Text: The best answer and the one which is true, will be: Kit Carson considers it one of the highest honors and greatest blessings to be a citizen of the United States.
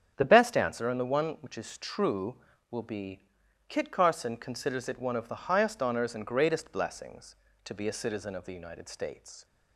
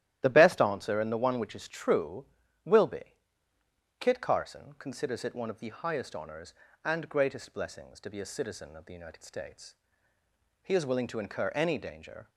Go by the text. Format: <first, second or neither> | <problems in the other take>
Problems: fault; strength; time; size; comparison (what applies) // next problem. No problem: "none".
first | starts louder than the rest; strong; until 1.2 s; 13 dB; strong in the first // goes on to say "He is willing to incur any danger"; from 10.6 s on; 1.6 s long